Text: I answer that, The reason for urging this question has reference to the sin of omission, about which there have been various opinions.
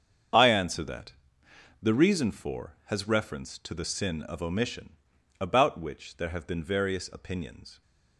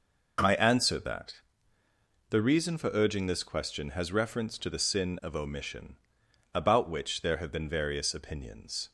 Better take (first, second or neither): second